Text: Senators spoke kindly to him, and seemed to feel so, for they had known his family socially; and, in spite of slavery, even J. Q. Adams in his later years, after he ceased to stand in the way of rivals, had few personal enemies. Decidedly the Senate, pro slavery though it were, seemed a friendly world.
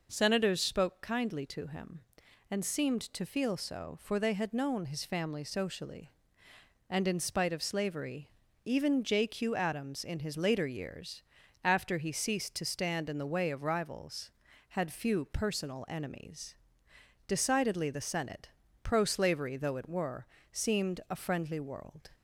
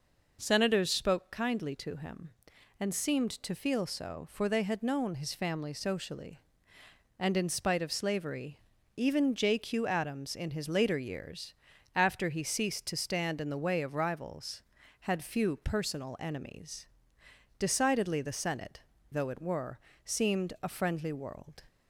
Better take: first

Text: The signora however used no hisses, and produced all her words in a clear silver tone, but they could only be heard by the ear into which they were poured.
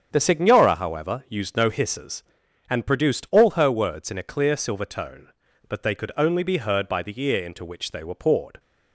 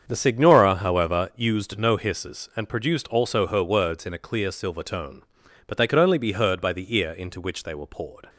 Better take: first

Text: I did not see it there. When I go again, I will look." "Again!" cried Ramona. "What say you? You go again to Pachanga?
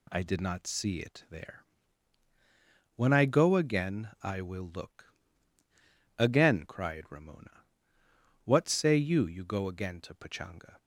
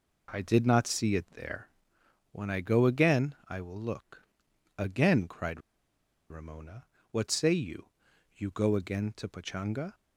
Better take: first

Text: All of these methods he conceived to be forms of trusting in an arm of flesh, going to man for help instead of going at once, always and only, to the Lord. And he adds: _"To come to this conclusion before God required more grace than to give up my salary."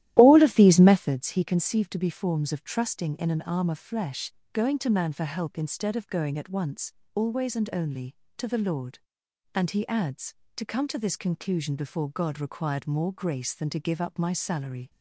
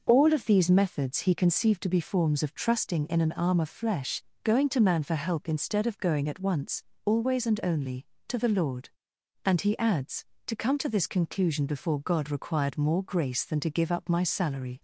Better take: second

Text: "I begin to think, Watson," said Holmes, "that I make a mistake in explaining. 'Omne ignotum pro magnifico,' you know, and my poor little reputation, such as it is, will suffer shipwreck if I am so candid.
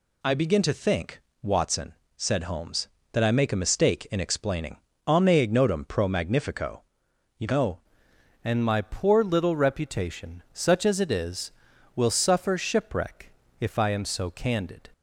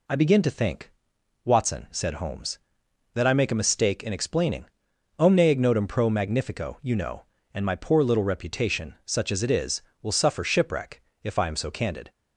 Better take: second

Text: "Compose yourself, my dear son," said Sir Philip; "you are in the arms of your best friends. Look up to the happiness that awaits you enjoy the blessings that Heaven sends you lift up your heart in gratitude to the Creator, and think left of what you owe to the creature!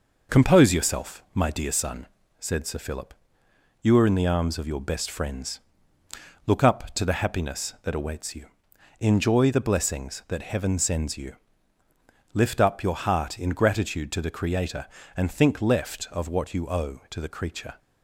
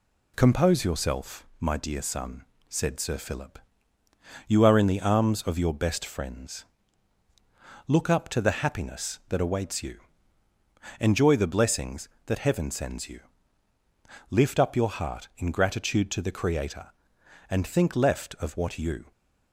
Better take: first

